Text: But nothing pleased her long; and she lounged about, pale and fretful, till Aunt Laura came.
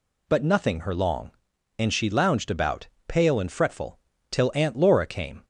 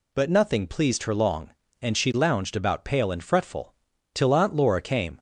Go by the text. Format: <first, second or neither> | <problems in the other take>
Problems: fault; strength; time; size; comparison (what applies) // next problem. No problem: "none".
second | skips "pleased"; at 0.8 s